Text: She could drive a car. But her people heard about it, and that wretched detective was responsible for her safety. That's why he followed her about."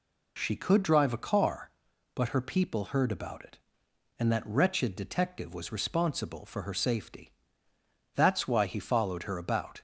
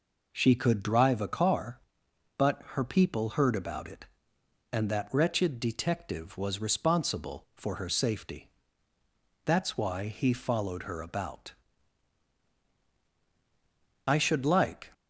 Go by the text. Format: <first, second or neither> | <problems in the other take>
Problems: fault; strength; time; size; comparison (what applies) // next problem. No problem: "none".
first | goes on to say "I should like"; noticeable; from 14.0 s on; 0.84 s long